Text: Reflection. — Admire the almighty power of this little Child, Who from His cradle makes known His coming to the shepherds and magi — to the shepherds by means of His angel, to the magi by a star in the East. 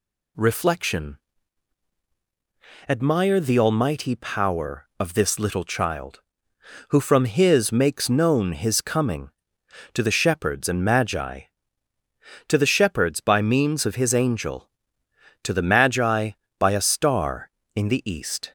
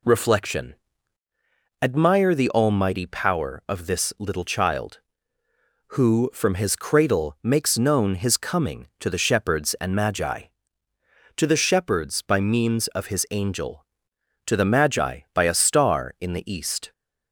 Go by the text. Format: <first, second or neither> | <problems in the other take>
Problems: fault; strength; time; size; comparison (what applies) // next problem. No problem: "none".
second | skips "cradle"; at 7.7 s